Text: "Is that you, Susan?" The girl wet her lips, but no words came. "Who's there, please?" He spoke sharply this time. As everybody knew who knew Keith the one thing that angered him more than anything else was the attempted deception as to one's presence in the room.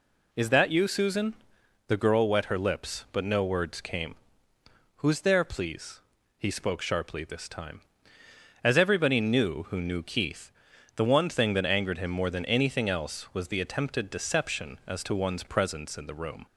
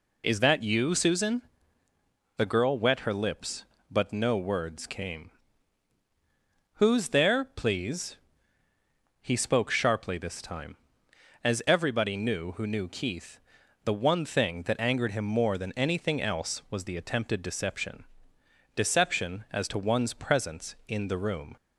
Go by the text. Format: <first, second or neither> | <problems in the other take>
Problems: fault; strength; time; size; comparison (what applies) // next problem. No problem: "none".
first | pauses between "Keith" and "the"; at 13.3 s; 0.44 s long; noticeable in the first // says "deception" twice; at 18.7 s